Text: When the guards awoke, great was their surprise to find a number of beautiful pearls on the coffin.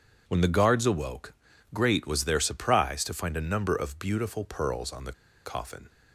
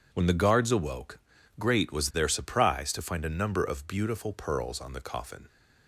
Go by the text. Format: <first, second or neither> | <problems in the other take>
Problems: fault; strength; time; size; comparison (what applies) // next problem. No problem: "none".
second | pauses between "the" and "coffin"; slight; at 5.1 s; 0.32 s long